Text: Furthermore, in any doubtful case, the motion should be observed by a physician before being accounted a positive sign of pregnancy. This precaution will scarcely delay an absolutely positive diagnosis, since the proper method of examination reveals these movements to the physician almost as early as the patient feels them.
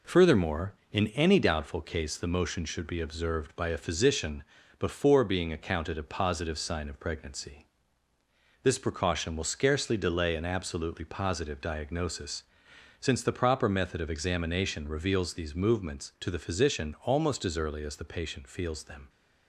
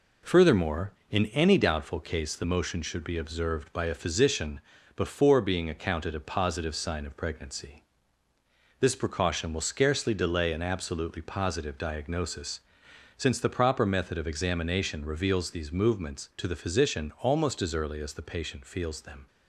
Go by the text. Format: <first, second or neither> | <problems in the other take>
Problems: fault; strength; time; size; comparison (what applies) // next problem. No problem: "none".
neither | pauses between "physician" and "before"; slight; the same in both